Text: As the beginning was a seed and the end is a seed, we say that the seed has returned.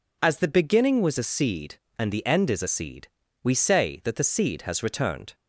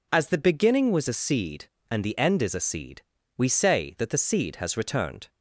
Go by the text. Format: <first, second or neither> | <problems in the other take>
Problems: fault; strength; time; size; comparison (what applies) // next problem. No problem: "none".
neither | none